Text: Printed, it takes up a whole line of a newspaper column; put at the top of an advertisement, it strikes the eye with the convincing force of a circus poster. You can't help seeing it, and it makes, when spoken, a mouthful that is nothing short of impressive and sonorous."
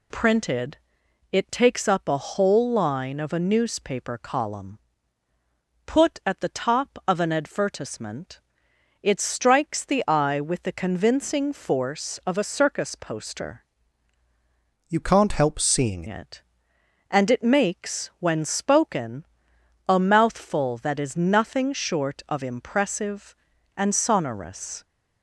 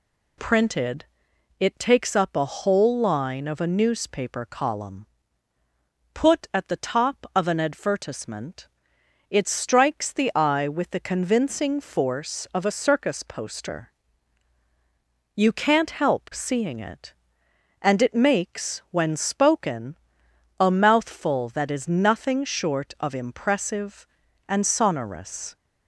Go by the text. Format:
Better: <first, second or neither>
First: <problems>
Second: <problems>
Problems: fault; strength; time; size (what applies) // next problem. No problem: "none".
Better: second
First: changes voice from "You" to "seeing"; from 14.8 to 16.0 s; 1.2 s long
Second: none